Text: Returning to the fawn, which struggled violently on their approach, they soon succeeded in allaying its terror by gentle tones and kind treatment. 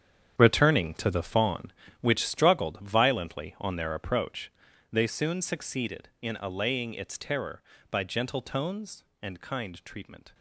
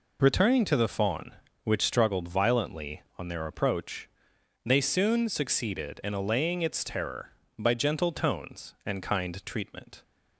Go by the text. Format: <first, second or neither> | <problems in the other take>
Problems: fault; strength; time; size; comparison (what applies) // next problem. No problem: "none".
second | gets quieter; strong; throughout; 13 dB